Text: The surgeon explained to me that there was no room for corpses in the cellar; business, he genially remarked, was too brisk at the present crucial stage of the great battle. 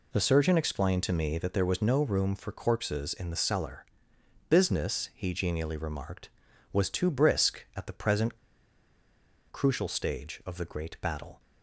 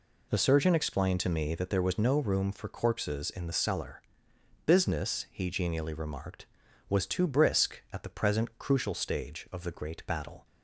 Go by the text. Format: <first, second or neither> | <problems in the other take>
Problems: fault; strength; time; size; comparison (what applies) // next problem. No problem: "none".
second | pauses between "present" and "crucial"; at 8.3 s; 1.1 s long